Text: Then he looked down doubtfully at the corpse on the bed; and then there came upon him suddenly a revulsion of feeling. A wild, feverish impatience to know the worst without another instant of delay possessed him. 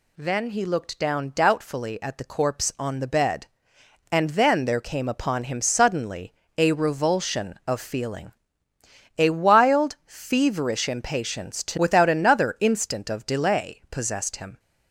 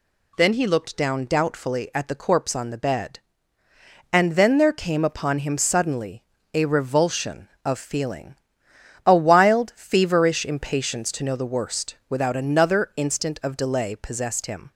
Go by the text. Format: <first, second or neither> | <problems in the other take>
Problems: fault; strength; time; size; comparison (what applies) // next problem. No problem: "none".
second | pauses between "suddenly" and "a"; slight; at 6.3 s; 0.22 s long; slight in the second // skips "know the worst"; at 11.7 s